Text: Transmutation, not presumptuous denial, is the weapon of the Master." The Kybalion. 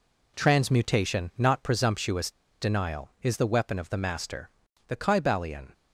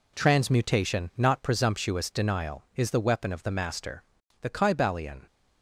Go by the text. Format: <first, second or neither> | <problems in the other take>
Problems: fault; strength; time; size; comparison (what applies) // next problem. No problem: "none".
second | pauses between "presumptuous" and "denial"; slight; at 2.2 s; 0.30 s long